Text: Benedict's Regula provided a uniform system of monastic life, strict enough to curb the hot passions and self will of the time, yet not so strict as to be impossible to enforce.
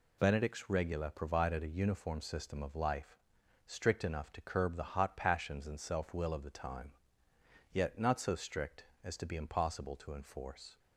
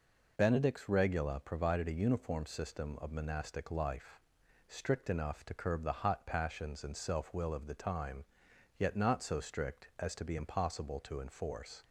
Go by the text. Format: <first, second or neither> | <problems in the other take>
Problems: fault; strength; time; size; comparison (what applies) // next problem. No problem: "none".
second | skips "monastic"; at 2.7 s